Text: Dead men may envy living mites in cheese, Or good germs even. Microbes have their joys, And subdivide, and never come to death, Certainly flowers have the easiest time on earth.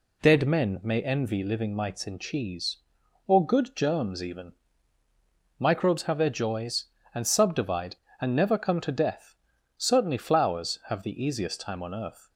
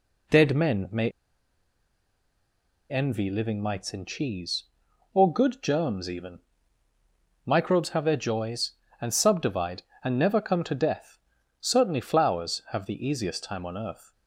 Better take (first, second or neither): first